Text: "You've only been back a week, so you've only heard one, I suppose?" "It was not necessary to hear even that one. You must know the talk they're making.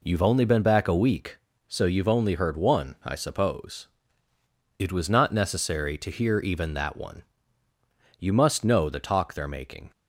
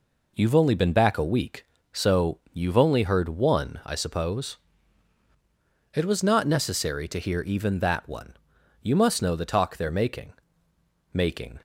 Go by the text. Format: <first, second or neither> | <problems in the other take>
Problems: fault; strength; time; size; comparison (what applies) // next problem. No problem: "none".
first | says "making" twice; at 11.1 s